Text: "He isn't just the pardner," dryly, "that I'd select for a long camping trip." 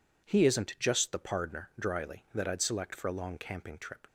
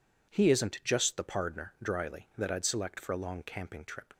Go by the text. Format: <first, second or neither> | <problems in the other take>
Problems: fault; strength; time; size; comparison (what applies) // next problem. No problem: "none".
neither | none